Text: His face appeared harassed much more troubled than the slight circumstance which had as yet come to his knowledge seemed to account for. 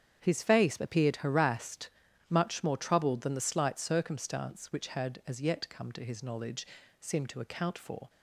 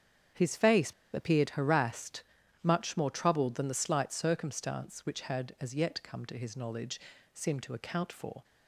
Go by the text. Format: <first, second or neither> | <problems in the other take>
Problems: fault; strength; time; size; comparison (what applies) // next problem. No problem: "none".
first | starts louder than the rest; strong; until 1.5 s; 8.5 dB; strong in the first // pauses between "face" and "appeared"; slight; at 0.9 s; 0.22 s long // pauses between "harassed" and "much"; at 2.2 s; 0.44 s long; also in the first // pauses between "knowledge" and "seemed"; slight; at 6.9 s; 0.36 s long; slight in the first